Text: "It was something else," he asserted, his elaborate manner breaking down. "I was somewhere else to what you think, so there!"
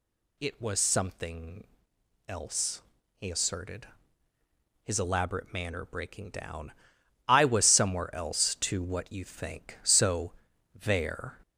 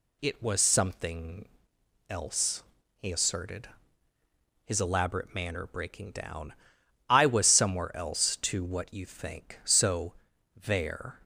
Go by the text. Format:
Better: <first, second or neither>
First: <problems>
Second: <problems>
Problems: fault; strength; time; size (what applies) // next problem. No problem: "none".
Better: second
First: gets louder; slight; throughout; 3.5 dB // pauses between "something" and "else"; noticeable; at 1.6 s; 0.62 s long // pauses between "so" and "there"; at 10.3 s; 0.40 s long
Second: pauses between "something" and "else"; noticeable; at 1.4 s; 0.62 s long // pauses between "so" and "there"; at 10.1 s; 0.40 s long